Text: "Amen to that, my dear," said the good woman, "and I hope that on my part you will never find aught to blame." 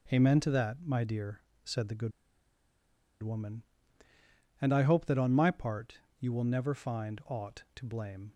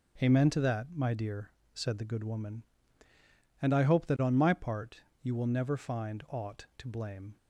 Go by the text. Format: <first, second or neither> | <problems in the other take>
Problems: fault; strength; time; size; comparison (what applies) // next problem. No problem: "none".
second | starts louder than the rest; strong; until 1.2 s; 7.5 dB; strong in the second // pauses between "good" and "woman"; at 2.1 s; 1.1 s long // pauses between "part" and "you"; slight; at 5.9 s; 0.20 s long; slight in the second